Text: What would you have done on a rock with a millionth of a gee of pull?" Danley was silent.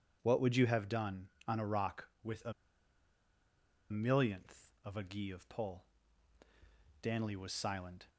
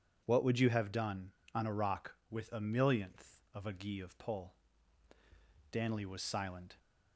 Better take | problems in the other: second | pauses between "a" and "millionth"; strong; at 2.5 s; 1.3 s long

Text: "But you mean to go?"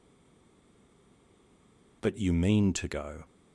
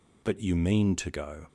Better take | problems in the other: second | stays silent before the first word; noticeable; until 2.0 s; 2.0 s long

